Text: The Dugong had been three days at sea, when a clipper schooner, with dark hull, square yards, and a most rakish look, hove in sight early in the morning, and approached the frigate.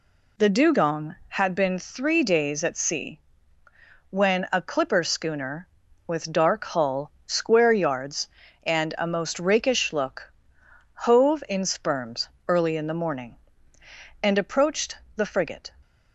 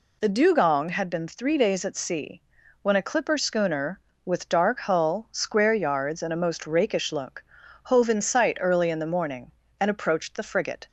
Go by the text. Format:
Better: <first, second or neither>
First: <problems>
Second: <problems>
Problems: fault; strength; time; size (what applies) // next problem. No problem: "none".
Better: second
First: says "sperms" for "sight"; at 11.6 s // pauses between "approached" and "the"; slight; at 14.9 s; 0.18 s long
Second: none